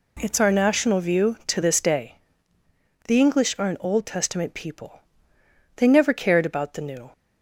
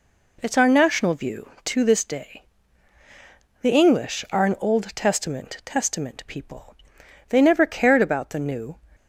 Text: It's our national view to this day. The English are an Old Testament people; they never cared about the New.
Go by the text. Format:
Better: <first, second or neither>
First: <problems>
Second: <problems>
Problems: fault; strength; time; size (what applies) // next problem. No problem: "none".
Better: first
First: none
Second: says "Testament" twice; at 5.6 s